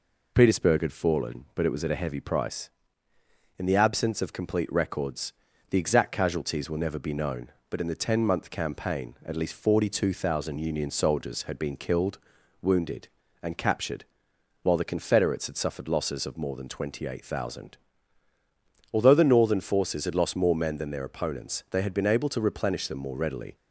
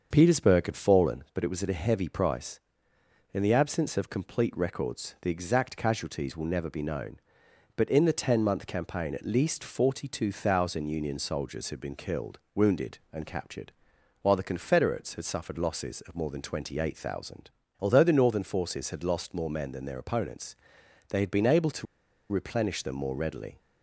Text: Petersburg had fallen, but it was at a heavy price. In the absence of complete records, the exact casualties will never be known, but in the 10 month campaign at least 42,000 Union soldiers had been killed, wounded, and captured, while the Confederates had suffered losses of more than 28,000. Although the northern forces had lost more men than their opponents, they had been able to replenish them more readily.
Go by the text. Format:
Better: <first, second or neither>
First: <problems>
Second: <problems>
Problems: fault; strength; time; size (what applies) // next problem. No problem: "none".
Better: first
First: none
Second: starts louder than the rest; until 1.1 s; 7 dB // pauses between "to" and "replenish"; noticeable; at 21.8 s; 0.46 s long